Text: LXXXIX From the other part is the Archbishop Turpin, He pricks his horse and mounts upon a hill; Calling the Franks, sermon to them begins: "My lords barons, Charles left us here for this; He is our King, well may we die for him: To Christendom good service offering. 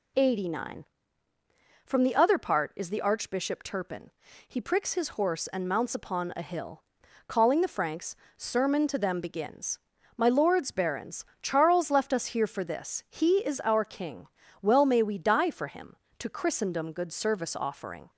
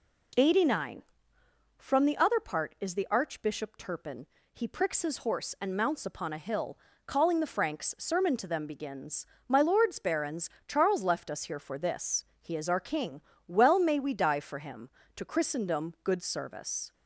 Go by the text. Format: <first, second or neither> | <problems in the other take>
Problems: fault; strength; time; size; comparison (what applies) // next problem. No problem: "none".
first | stops before "offering"; at 16.9 s